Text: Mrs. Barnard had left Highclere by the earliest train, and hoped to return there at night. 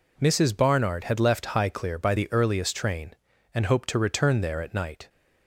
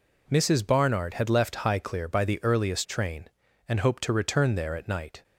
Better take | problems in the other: neither | none

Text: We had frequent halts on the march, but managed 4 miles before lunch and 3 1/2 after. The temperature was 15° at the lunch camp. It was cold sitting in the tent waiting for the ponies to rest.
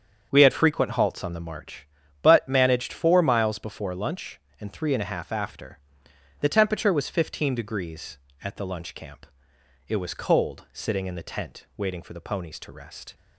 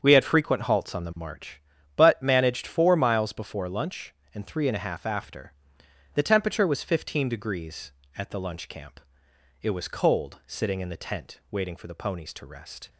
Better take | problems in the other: neither | starts louder than the rest; the same in both

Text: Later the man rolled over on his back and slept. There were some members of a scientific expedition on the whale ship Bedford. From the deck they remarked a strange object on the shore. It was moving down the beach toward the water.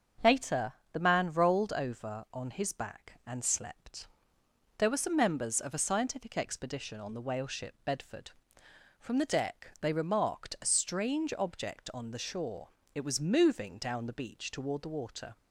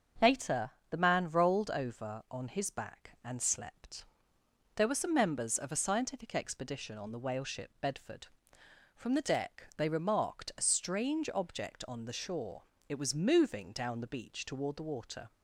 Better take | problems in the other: neither | starts louder than the rest; the same in both // pauses between "Later" and "the"; slight; the same in both

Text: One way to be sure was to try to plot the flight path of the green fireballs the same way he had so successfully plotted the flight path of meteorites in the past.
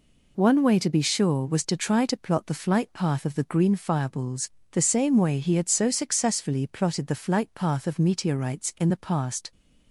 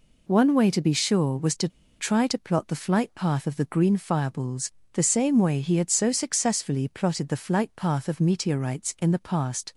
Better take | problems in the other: first | pauses between "to" and "try"; slight; at 1.6 s; 0.29 s long // pauses between "fireballs" and "the"; slight; at 4.7 s; 0.22 s long; slight in the first

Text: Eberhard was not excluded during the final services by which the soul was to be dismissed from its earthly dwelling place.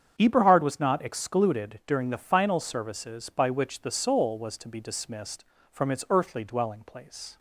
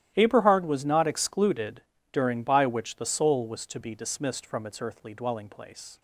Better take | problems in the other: first | starts louder than the rest; strong; until 1.1 s; 13.5 dB; strong in the first // pauses between "excluded" and "during"; slight; at 1.8 s; 0.30 s long // skips "the final services"; at 2.4 s

